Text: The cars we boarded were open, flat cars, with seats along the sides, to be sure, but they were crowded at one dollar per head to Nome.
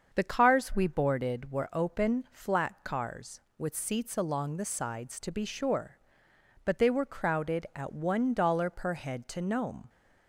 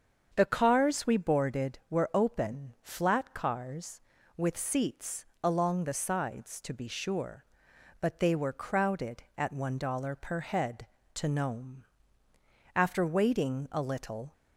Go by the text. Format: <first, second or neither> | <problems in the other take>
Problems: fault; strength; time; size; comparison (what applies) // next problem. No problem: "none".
first | starts louder than the rest; strong; until 1.3 s; 7 dB; also in the first // pauses between "seats" and "along"; slight; at 5.2 s; 0.16 s long // goes on to say "After waiting a little"; from 12.7 s on; 1.5 s long